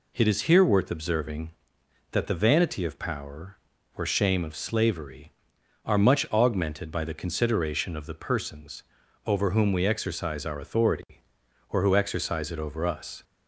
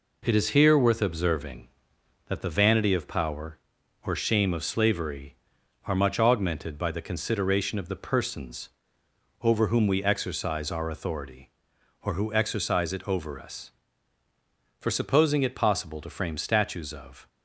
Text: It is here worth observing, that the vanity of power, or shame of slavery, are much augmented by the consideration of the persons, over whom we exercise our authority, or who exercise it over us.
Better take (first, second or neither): first